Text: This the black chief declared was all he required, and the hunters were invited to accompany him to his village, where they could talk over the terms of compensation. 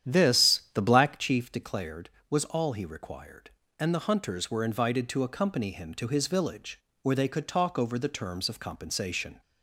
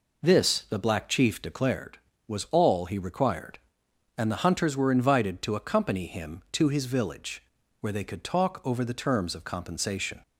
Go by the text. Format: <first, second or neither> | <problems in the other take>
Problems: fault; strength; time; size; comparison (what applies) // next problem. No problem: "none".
second | starts louder than the rest; strong; until 1.3 s; 10 dB